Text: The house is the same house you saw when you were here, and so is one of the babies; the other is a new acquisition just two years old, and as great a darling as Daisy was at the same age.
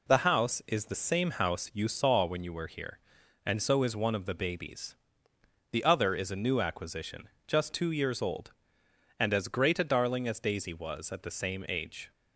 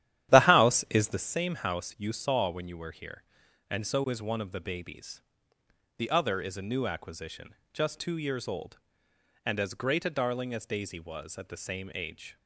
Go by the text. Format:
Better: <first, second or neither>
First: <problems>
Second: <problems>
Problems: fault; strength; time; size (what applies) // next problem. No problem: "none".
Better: first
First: pauses between "acquisition" and "just"; slight; at 7.2 s; 0.20 s long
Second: starts louder than the rest; strong; until 1.3 s; 11.5 dB // pauses between "acquisition" and "just"; slight; at 7.5 s; 0.20 s long